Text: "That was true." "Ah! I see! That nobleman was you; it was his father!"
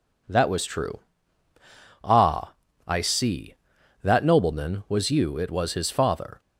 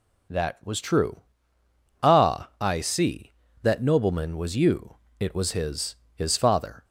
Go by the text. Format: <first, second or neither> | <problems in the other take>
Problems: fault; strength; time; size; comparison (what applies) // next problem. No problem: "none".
first | says "his" twice; at 6.1 s